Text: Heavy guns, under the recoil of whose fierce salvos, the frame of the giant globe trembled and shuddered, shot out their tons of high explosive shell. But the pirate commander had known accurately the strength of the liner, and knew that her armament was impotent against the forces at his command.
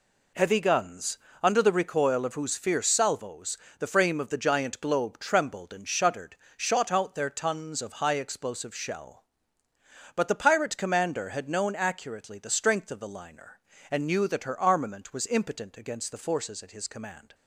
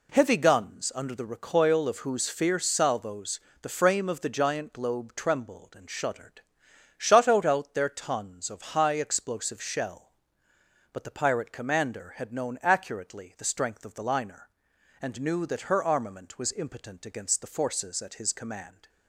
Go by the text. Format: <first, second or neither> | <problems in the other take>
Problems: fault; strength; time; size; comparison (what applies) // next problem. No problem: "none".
first | says "out" twice; at 7.4 s